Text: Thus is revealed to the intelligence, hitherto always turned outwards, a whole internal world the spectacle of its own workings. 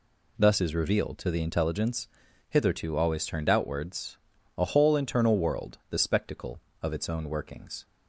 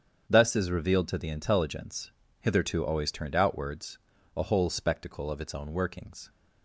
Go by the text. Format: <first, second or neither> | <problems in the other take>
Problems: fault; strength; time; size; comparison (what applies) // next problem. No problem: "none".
first | starts louder than the rest; strong; until 1.2 s; 7.5 dB // skips "internal world the"; at 4.6 s